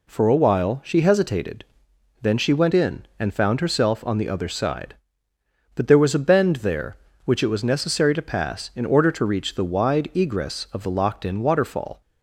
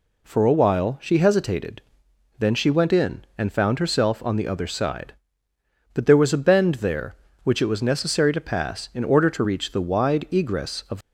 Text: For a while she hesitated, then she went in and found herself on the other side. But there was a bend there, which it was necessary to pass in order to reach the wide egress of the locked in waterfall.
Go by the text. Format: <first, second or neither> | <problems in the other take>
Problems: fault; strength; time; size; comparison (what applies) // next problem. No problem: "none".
first | stops before "the locked in waterfall"; at 11.0 s